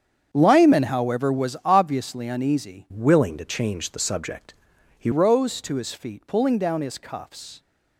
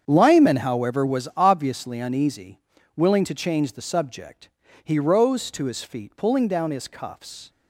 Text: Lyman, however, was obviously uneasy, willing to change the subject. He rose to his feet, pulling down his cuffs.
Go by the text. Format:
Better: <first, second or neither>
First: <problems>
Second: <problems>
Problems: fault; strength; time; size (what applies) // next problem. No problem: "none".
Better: second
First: starts louder than the rest; strong; until 1.3 s; 7.5 dB // changes voice from "willing" to "He"; from 2.9 to 5.1 s; 2.2 s long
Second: starts louder than the rest; strong; until 1.0 s; 7.5 dB